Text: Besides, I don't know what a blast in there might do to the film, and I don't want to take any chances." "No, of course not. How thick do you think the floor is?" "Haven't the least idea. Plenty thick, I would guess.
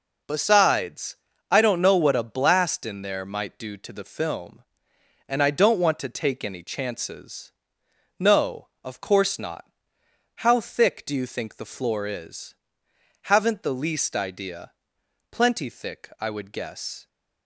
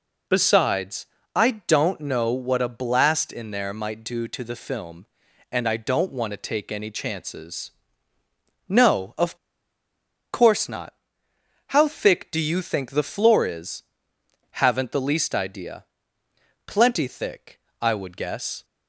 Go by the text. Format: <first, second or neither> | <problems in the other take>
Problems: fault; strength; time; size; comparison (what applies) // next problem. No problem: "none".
first | pauses between "of" and "course"; noticeable; at 9.3 s; 0.96 s long